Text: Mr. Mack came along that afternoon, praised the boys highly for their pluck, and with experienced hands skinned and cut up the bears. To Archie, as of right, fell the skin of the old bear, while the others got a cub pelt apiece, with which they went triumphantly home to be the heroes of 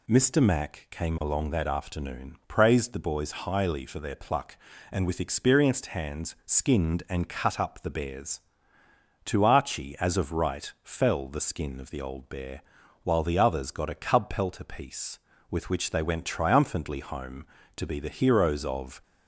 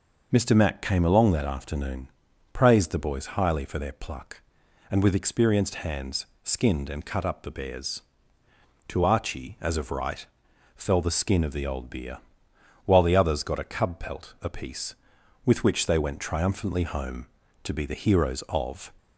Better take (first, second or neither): first